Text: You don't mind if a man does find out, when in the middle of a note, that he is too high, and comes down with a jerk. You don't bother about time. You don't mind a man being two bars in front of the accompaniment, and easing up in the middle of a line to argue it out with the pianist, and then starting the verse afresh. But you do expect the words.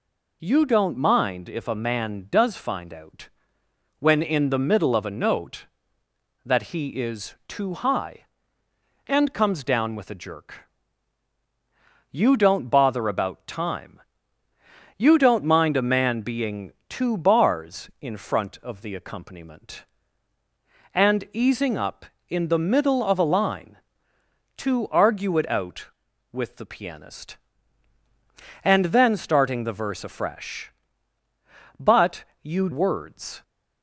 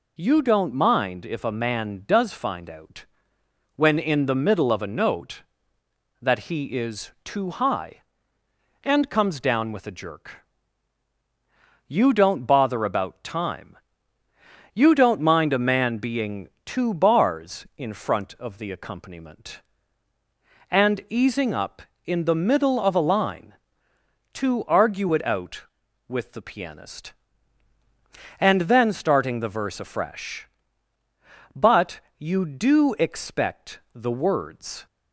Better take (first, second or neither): second